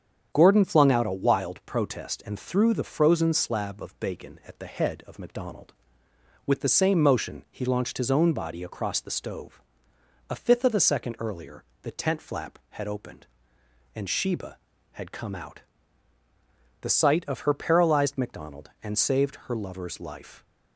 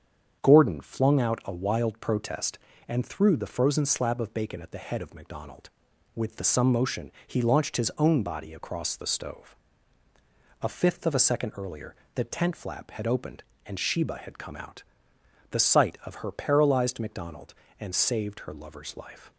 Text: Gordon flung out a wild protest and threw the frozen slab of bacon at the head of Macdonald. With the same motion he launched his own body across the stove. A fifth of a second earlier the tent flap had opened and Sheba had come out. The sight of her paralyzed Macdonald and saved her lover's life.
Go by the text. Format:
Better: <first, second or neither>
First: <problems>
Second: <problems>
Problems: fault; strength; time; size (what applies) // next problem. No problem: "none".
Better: first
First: starts louder than the rest; strong; until 1.3 s; 8 dB // pauses between "earlier" and "the"; slight; at 11.6 s; 0.18 s long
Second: starts louder than the rest; strong; until 1.4 s; 7.5 dB // says "some" for "same"; at 6.4 s // pauses between "motion" and "he"; slight; at 7.1 s; 0.16 s long // pauses between "earlier" and "the"; slight; at 11.9 s; 0.20 s long